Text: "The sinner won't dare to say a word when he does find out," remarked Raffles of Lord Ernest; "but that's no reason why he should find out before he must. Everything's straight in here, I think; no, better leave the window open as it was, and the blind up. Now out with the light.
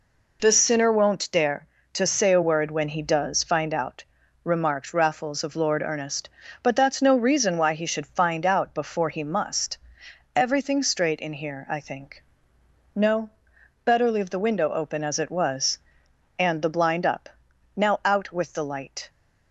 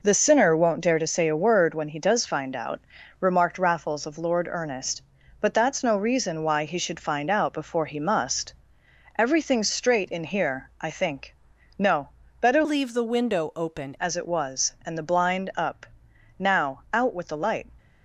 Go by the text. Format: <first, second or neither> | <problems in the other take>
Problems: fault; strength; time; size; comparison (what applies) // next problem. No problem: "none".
first | changes voice from "leave" to "open"; from 12.6 to 13.9 s; 1.3 s long